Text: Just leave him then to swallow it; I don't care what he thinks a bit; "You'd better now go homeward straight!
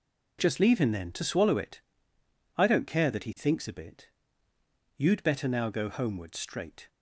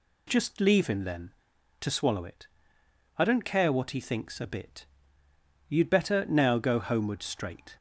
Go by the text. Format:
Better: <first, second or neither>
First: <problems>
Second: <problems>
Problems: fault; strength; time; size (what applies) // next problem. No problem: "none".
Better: second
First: says "that" for "what"; at 3.0 s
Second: none